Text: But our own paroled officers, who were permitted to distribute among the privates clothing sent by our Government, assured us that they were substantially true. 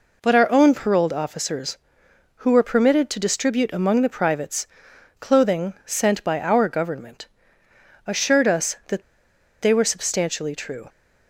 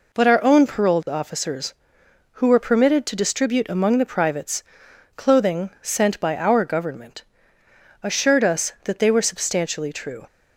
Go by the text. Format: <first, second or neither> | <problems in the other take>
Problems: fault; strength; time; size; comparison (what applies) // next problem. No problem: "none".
second | pauses between "privates" and "clothing"; noticeable; at 4.6 s; 0.54 s long; noticeable in the second // pauses between "that" and "they"; noticeable; at 9.0 s; 0.60 s long